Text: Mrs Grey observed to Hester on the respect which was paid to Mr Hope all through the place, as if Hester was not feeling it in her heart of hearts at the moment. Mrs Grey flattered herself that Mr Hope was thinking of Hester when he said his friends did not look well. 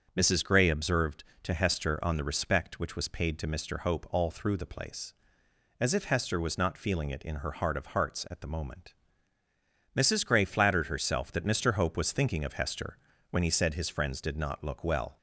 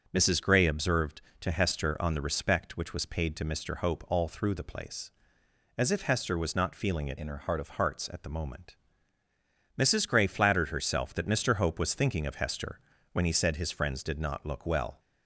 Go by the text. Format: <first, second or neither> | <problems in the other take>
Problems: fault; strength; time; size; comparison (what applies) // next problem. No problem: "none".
first | starts louder than the rest; until 1.1 s; 6 dB; also in the first // changes voice from "in" to "of"; from 7.1 to 7.6 s; 0.5 s long // pauses between "Hester" and "when"; slight; at 12.7 s; 0.32 s long; slight in the first